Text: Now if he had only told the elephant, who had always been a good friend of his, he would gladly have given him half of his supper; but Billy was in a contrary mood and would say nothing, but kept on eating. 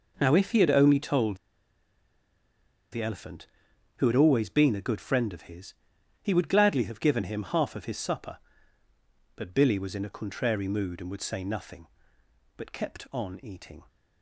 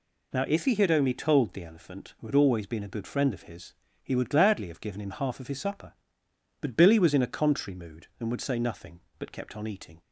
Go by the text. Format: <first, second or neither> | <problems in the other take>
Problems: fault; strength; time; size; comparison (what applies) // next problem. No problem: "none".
second | pauses between "told" and "the"; strong; at 1.3 s; 1.5 s long